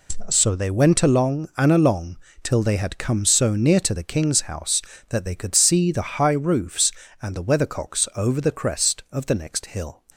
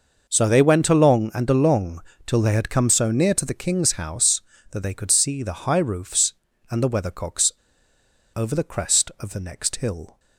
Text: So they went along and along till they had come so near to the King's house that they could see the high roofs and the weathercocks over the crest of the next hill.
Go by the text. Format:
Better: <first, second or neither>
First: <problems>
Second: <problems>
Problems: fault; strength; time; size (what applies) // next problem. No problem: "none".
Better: first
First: pauses between "along" and "till"; slight; at 2.1 s; 0.26 s long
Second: pauses between "along" and "till"; slight; at 2.0 s; 0.24 s long // pauses between "weathercocks" and "over"; noticeable; at 7.5 s; 0.84 s long